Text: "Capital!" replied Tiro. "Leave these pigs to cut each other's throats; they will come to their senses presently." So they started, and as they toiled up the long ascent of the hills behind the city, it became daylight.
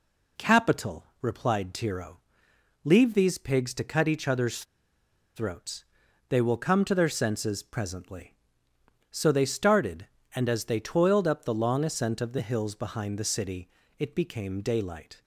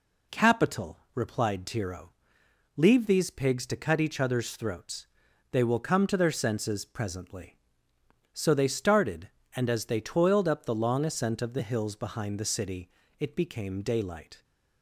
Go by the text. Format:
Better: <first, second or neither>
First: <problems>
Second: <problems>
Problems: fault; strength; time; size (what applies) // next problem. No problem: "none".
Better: second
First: pauses between "other's" and "throats"; noticeable; at 4.6 s; 0.72 s long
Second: none